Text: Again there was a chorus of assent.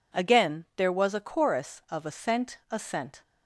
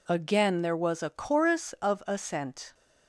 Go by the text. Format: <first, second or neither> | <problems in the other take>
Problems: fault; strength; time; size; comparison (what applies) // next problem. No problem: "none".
second | says "assent" twice; at 2.6 s